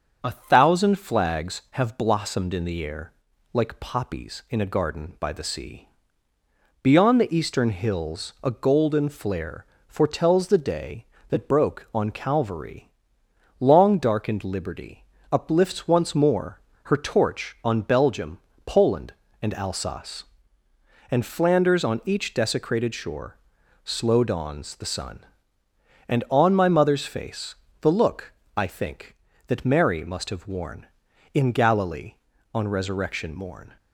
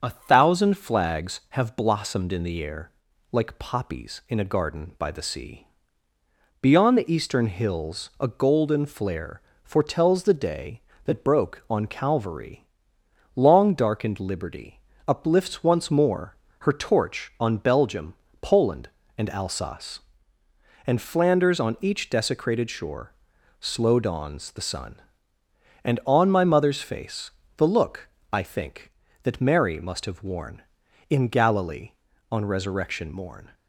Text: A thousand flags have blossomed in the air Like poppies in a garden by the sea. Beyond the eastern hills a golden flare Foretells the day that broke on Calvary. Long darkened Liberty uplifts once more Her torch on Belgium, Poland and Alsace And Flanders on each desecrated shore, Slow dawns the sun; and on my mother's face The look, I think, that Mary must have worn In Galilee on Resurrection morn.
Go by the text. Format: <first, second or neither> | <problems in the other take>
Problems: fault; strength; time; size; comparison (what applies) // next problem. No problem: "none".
neither | starts louder than the rest; the same in both // pauses between "air" and "Like"; the same in both // pauses between "flare" and "Foretells"; slight; the same in both // pauses between "Liberty" and "uplifts"; slight; the same in both // pauses between "more" and "Her"; slight; the same in both // pauses between "face" and "The"; slight; the same in both